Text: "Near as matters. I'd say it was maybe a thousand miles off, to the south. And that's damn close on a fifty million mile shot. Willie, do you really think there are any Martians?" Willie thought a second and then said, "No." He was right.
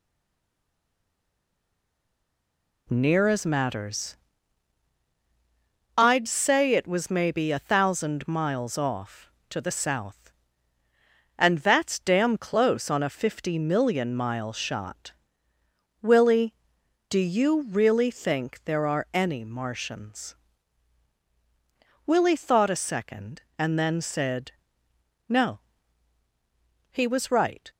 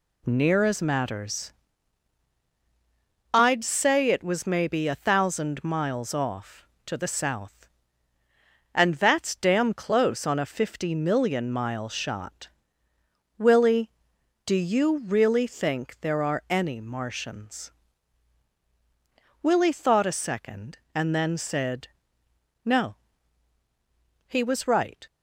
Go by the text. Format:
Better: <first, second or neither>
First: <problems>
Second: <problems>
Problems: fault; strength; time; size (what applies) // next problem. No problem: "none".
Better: second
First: stays silent before the first word; strong; until 2.8 s; 2.8 s long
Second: none